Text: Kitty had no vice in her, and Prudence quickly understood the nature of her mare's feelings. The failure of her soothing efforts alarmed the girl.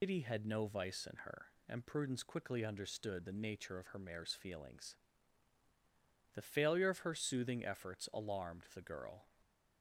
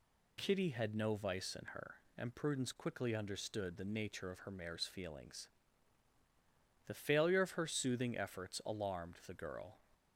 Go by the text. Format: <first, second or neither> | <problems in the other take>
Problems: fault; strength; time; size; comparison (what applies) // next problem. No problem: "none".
second | loses the start of "Kitty"; at 0.0 s; 130 ms